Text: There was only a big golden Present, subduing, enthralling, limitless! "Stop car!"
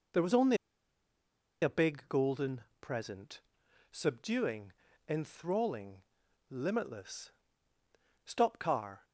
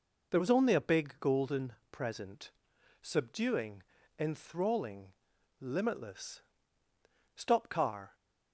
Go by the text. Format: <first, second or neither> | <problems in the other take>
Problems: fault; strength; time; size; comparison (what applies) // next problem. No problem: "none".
second | pauses between "only" and "a"; at 0.5 s; 1.0 s long // pauses between "golden" and "Present"; slight; at 2.6 s; 0.18 s long; slight in the second